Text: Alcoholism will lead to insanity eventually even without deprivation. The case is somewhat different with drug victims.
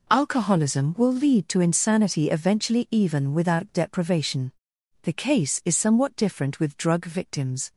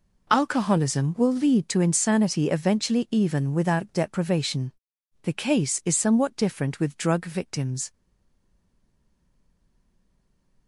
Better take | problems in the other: first | stays silent after the last word; strong; from 7.9 s on; 2.7 s long

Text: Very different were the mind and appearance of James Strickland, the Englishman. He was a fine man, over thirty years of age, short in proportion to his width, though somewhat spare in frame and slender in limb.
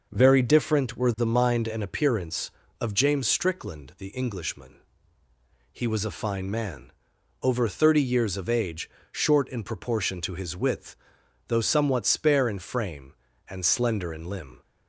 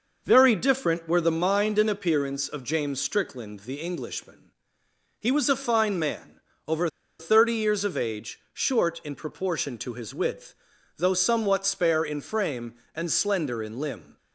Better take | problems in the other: first | pauses between "over" and "thirty"; slight; at 6.8 s; 0.30 s long

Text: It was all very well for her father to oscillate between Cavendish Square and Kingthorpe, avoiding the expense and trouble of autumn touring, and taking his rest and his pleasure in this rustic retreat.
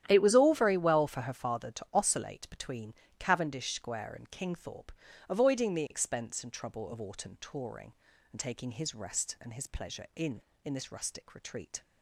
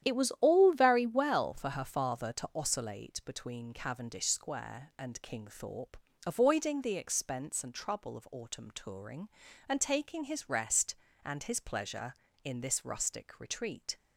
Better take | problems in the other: second | starts louder than the rest; strong; until 1.0 s; 11 dB; strong in the second // pauses between "between" and "Cavendish"; slight; at 2.9 s; 0.26 s long // says "in" twice; at 10.6 s

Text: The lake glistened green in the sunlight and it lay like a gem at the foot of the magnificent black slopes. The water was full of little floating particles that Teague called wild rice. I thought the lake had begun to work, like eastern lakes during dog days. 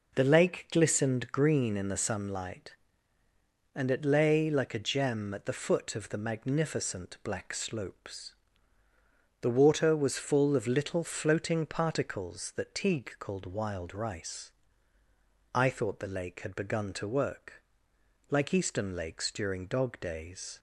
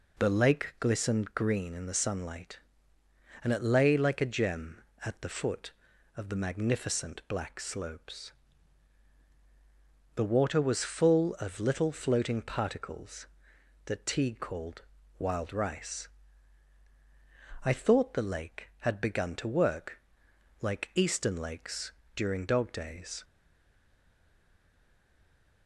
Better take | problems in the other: first | pauses between "called" and "wild"; at 14.8 s; 0.38 s long // pauses between "lakes" and "during"; slight; at 21.9 s; 0.24 s long // stays silent after the last word; from 23.2 s on; 2.4 s long

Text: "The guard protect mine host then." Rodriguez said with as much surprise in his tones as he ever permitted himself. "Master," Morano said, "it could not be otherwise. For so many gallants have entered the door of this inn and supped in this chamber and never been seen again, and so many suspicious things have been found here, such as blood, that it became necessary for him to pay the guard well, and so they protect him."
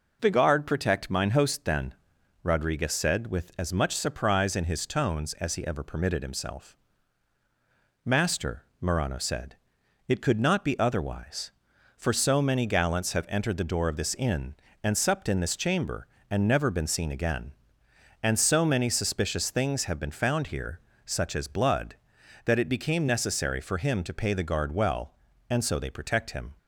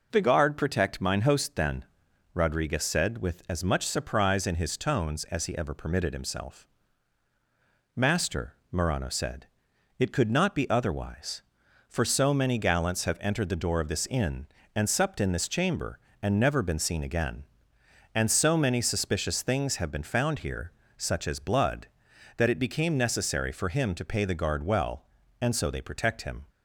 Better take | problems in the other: neither | none

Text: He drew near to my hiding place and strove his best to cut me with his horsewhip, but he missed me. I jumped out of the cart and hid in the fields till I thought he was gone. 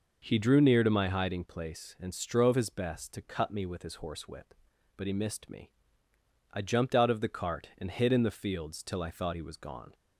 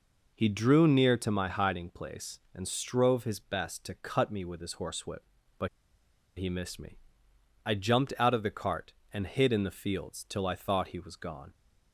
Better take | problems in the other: first | pauses between "but" and "he"; noticeable; at 5.6 s; 0.70 s long

